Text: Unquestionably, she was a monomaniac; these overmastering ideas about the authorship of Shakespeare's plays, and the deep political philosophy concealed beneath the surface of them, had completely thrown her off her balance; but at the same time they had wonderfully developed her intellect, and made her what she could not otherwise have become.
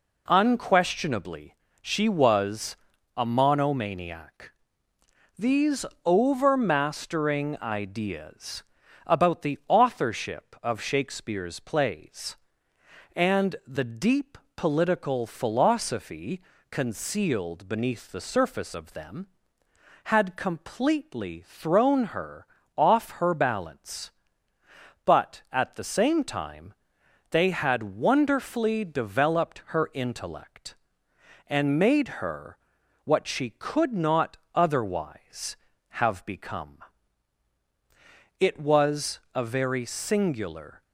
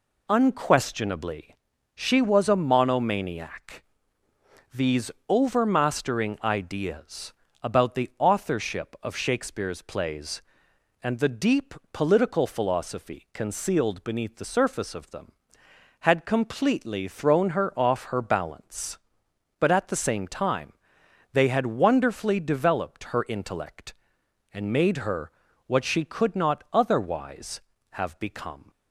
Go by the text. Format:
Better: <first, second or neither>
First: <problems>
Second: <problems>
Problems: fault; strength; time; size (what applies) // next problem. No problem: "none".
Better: second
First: pauses between "was" and "a"; at 2.7 s; 0.40 s long // pauses between "these" and "overmastering"; slight; at 5.8 s; 0.20 s long // pauses between "ideas" and "about"; at 8.6 s; 0.40 s long // pauses between "deep" and "political"; slight; at 14.3 s; 0.20 s long // pauses between "philosophy" and "concealed"; slight; at 16.4 s; 0.30 s long // pauses between "her" and "off"; slight; at 22.4 s; 0.32 s long // pauses between "time" and "they"; noticeable; at 26.7 s; 0.56 s long // pauses between "her" and "what"; noticeable; at 32.5 s; 0.48 s long // pauses between "not" and "otherwise"; slight; at 34.3 s; 0.16 s long // goes on to say "It was a very singular"; strong; from 38.3 s on; 2.4 s long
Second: pauses between "these" and "overmastering"; slight; at 5.1 s; 0.16 s long // pauses between "ideas" and "about"; slight; at 7.3 s; 0.28 s long // pauses between "deep" and "political"; slight; at 11.7 s; 0.18 s long // pauses between "time" and "they"; noticeable; at 20.7 s; 0.60 s long // pauses between "her" and "what"; slight; at 25.3 s; 0.34 s long